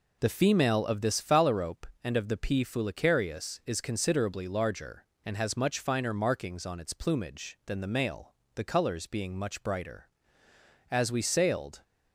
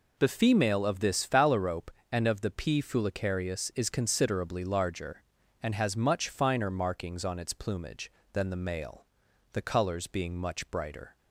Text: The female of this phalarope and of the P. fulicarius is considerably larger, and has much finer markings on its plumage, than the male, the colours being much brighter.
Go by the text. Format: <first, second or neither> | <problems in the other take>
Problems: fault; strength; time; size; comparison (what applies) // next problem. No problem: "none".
second | goes on to say "As we sailed"; noticeable; from 10.9 s on; 0.92 s long